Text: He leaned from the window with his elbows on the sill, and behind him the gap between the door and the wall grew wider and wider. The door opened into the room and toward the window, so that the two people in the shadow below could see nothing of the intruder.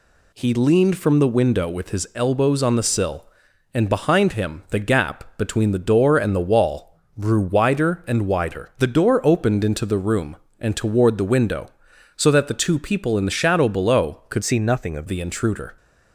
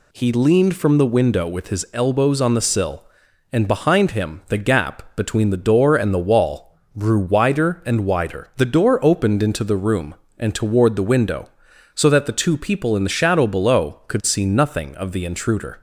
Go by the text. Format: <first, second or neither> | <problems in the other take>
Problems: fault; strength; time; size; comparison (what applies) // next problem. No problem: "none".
second | pauses between "wall" and "grew"; slight; at 6.9 s; 0.20 s long; slight in the second // changes voice from "see" to "of"; from 14.4 to 15.0 s; 0.6 s long